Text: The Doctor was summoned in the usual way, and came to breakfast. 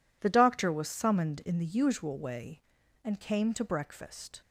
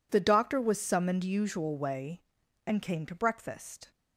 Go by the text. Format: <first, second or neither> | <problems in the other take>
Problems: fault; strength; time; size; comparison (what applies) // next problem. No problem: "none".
first | skips "in the"; at 1.2 s